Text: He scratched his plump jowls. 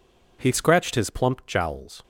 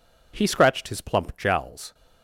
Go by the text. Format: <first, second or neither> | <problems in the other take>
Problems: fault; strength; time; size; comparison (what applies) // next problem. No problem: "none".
neither | none